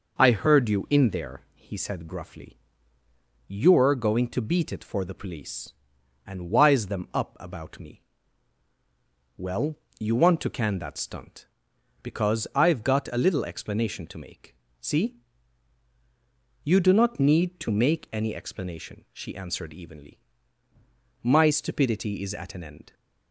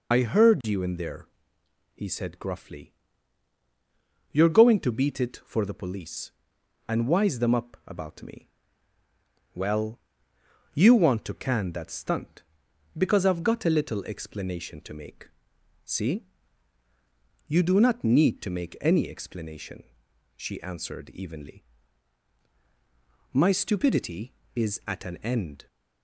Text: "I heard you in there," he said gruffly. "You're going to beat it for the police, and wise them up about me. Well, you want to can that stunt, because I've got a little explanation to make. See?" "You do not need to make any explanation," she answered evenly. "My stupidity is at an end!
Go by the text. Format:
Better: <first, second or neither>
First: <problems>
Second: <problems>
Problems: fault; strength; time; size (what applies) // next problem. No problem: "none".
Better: first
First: none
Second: loses the start of "I"; at 0.1 s; 50 ms